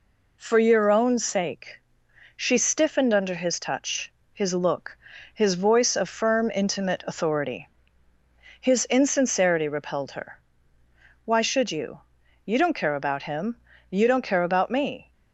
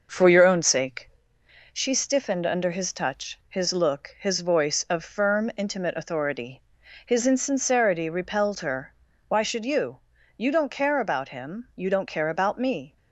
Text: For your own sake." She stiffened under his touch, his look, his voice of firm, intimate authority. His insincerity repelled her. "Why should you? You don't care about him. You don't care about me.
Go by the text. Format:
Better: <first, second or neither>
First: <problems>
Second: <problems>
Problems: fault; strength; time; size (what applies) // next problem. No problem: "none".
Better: first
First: none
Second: starts louder than the rest; noticeable; until 1.2 s; 6 dB